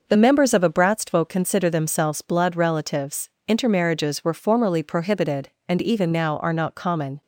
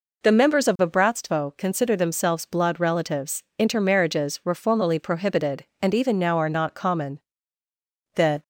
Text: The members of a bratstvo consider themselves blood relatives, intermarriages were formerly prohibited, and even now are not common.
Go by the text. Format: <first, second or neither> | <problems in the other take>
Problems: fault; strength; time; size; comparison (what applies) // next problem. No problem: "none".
first | goes on to say "The"; slight; from 8.1 s on; 0.28 s long